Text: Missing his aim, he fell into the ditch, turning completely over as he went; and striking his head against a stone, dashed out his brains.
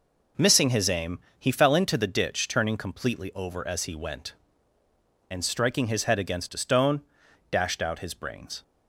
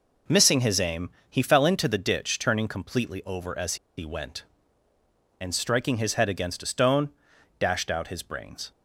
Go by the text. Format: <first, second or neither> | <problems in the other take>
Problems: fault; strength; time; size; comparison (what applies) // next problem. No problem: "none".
first | pauses between "as" and "he"; slight; at 3.7 s; 0.21 s long